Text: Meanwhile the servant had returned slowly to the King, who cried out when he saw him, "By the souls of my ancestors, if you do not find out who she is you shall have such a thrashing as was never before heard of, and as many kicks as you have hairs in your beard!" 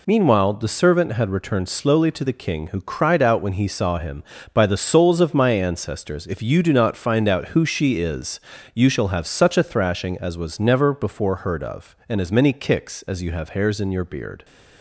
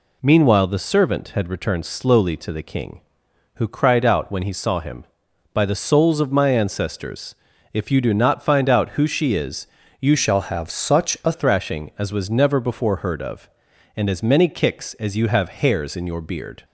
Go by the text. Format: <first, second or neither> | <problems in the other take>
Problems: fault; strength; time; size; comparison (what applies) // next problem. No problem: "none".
first | pauses between "is" and "you"; slight; at 9.6 s; 0.36 s long; slight in the first // changes voice from "shall" to "a"; from 10.1 to 11.3 s; 1.2 s long